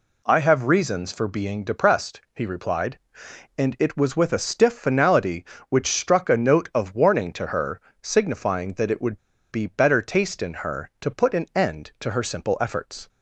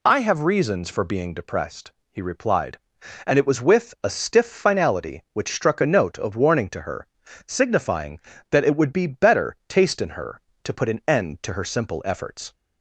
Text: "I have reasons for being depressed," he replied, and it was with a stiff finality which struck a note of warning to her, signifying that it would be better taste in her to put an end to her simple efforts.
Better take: second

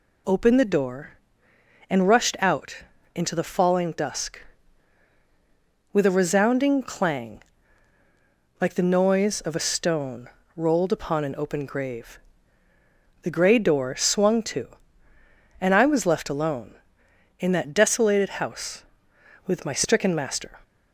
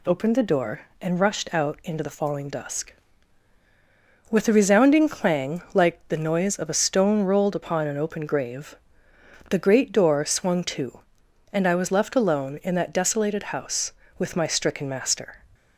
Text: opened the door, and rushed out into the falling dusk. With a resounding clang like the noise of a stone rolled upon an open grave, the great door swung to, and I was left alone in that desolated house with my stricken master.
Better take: second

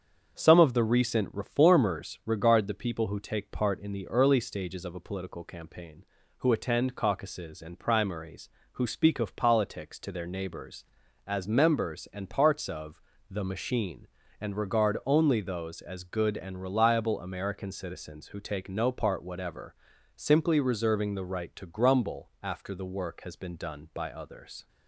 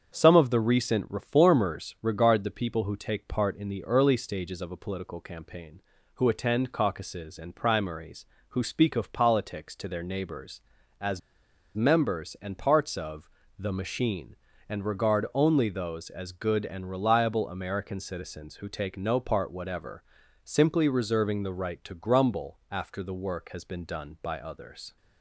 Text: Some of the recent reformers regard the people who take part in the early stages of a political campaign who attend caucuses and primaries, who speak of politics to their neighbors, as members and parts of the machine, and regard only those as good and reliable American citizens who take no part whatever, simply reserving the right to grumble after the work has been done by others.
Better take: first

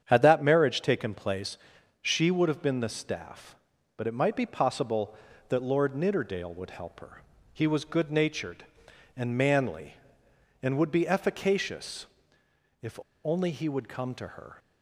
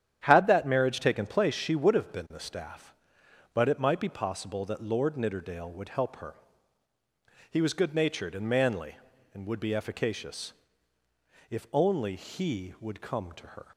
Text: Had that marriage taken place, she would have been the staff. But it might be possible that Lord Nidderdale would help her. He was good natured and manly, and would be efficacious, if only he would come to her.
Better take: second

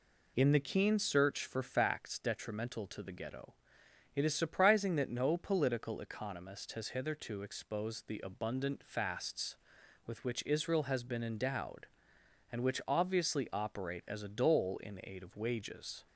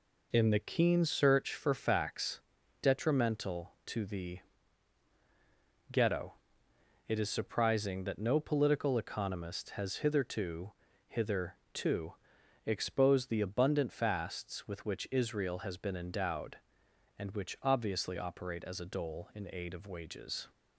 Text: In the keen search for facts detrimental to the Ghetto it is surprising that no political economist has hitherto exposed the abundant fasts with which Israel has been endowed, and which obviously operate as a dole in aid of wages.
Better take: first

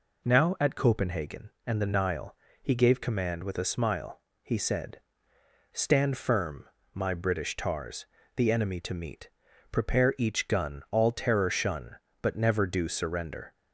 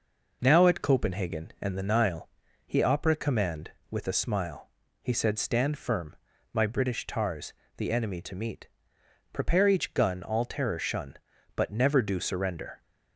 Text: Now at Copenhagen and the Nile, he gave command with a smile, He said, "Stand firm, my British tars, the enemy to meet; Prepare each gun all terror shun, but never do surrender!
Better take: first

